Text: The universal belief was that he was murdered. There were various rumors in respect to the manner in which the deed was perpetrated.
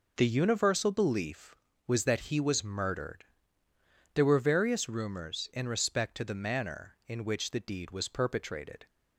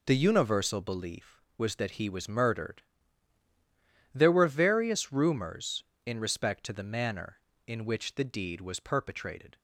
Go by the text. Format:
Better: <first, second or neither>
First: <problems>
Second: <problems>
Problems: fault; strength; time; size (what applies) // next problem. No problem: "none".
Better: neither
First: none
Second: none